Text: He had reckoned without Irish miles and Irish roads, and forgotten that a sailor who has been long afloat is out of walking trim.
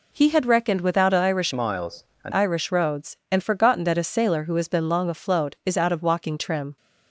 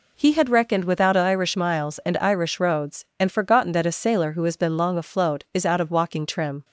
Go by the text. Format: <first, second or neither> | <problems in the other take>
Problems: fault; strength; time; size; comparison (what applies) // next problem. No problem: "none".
second | changes voice from "miles" to "and"; from 1.5 to 2.3 s; 0.8 s long